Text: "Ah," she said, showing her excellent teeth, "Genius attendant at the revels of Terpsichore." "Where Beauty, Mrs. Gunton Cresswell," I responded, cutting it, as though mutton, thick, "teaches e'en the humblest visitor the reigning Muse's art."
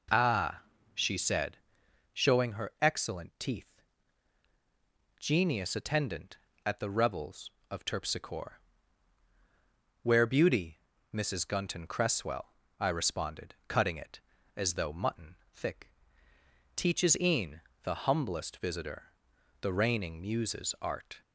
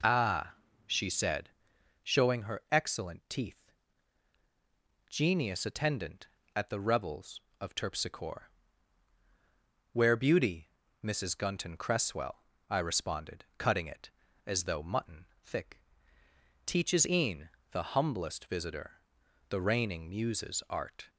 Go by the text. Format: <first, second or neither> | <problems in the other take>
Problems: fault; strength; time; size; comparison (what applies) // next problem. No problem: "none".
neither | pauses between "e'en" and "the"; slight; the same in both // pauses between "visitor" and "the"; noticeable; the same in both